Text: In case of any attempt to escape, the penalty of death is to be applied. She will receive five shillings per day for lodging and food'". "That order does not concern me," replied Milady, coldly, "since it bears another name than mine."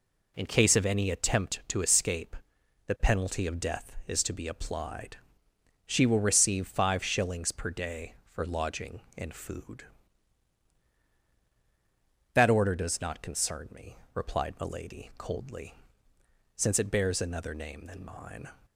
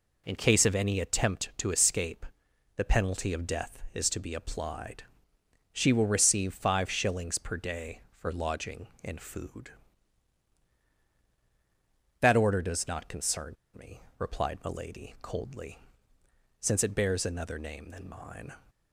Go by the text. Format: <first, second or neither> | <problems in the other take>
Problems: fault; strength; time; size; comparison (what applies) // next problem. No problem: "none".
first | pauses between "concern" and "me"; slight; at 13.5 s; 0.20 s long